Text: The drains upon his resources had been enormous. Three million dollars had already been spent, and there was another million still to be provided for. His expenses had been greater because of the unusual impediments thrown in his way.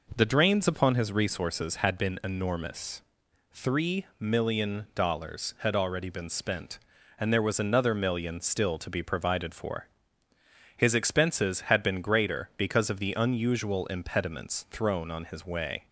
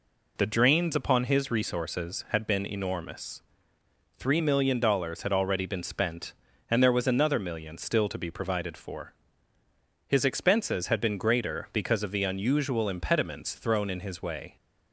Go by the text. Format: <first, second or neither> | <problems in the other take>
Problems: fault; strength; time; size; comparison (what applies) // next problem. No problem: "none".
second | says "on" for "in"; at 15.0 s